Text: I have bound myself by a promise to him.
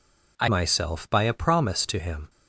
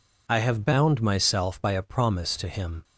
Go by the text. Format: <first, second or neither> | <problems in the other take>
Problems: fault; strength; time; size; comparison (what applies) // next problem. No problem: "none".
second | skips "have bound"; at 0.4 s